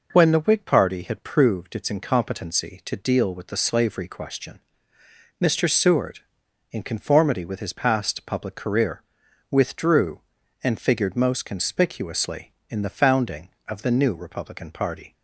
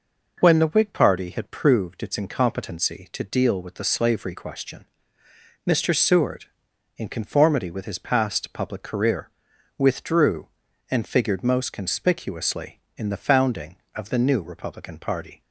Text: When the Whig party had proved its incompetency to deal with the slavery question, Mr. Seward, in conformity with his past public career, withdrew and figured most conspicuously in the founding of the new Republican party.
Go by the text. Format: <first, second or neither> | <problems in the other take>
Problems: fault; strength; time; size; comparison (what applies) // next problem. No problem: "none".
neither | none